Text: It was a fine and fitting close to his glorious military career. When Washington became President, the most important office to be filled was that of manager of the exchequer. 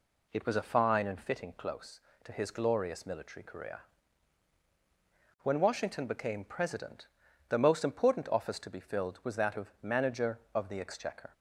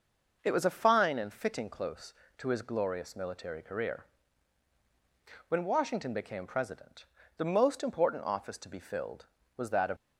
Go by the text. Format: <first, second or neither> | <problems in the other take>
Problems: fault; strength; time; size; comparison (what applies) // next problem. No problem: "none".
first | stops before "manager of the exchequer"; at 9.9 s